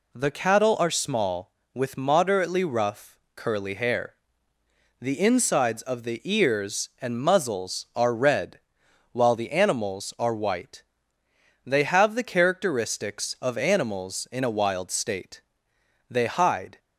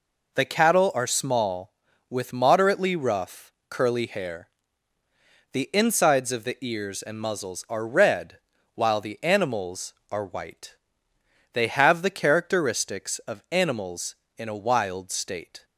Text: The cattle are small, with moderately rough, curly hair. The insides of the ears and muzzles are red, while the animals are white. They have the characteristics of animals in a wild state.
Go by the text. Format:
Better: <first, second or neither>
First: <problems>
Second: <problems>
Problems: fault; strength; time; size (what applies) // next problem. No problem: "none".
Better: second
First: goes on to say "They hide"; noticeable; from 16.0 s on; 0.70 s long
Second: none